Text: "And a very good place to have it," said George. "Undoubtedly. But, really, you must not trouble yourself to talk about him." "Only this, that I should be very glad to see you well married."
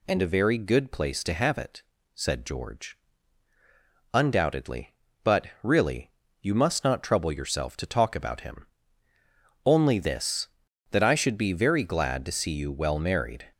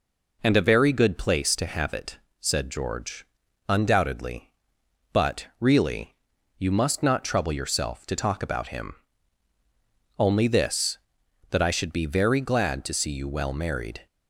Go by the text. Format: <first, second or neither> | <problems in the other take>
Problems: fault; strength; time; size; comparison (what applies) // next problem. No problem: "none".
neither | none